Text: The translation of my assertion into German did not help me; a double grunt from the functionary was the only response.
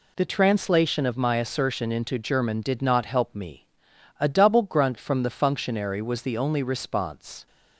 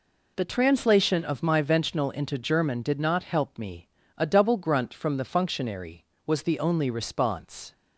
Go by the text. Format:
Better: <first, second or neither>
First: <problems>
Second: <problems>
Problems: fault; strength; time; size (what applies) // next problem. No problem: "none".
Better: first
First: none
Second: says "ventional" for "assertion"; at 1.6 s